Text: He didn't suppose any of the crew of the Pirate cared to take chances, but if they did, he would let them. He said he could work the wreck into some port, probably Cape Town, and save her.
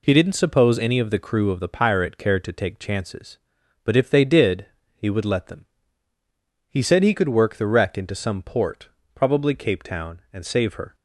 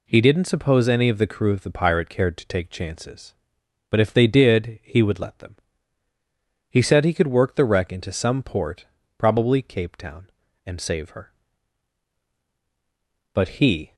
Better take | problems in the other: first | goes on to say "But he"; noticeable; from 13.3 s on; 0.62 s long

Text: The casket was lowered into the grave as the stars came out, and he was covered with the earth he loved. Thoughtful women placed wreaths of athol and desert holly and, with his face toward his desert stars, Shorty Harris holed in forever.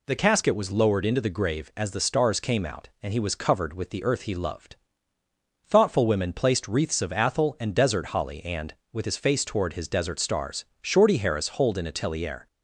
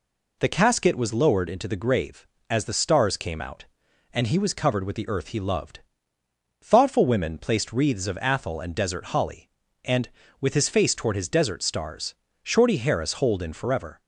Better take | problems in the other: second | says "atelier" for "forever"; at 11.8 s

